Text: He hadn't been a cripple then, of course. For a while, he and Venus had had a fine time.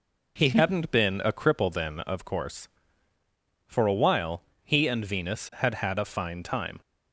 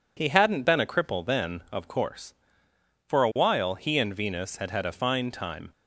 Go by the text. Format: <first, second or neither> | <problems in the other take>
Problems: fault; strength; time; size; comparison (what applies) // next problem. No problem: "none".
neither | none